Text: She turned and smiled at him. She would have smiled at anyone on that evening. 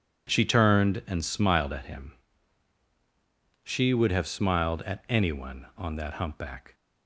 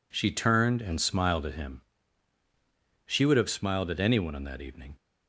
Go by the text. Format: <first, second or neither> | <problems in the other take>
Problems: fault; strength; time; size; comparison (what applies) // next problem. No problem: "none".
second | says "humpback" for "evening"; at 6.1 s